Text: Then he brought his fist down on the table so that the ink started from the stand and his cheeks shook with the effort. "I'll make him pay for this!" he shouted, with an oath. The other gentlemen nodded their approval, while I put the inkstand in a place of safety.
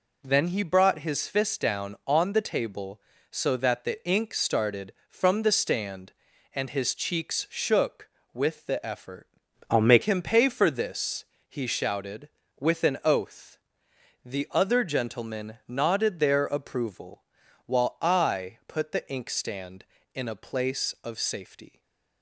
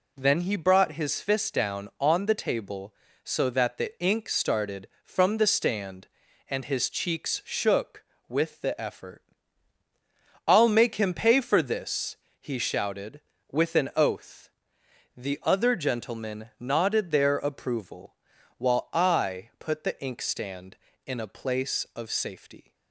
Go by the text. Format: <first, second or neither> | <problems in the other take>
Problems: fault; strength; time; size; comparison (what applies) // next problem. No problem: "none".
second | changes voice from "I'll" to "make"; from 9.6 to 10.0 s; 0.4 s long // stays silent after the last word; slight; from 21.6 s on; 0.6 s long